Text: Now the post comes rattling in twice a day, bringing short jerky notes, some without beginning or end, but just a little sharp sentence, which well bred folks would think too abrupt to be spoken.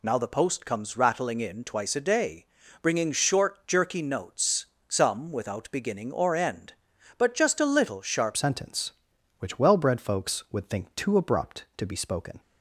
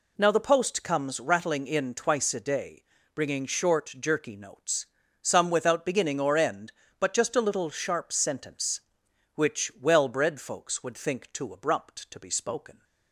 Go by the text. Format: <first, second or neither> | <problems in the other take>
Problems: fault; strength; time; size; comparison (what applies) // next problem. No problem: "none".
second | changes voice at "sentence"; from 8.3 s on; 4.1 s long